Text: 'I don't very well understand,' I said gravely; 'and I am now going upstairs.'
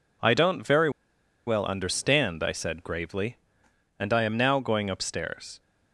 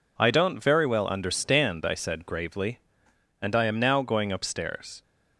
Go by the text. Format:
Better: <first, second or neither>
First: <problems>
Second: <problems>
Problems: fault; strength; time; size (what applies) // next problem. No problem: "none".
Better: second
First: pauses between "very" and "well"; noticeable; at 0.8 s; 0.57 s long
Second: none